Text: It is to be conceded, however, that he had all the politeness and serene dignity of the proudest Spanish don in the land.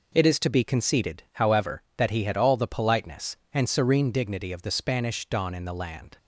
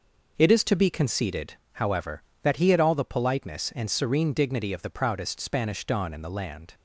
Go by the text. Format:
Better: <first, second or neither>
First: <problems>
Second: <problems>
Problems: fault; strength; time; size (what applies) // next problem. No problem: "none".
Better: second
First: skips "proudest"; at 4.7 s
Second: none